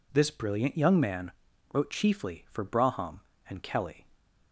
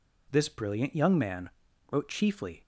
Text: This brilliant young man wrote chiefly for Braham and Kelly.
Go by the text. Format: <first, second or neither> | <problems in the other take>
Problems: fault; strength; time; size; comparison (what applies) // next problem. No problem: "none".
first | pauses between "man" and "wrote"; at 1.4 s; 0.42 s long; also in the first // stops before "for Braham and Kelly"; at 2.6 s